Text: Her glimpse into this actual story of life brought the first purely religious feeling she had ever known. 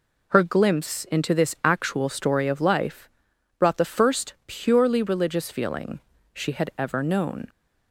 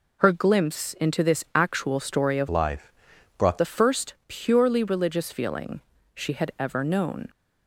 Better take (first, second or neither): first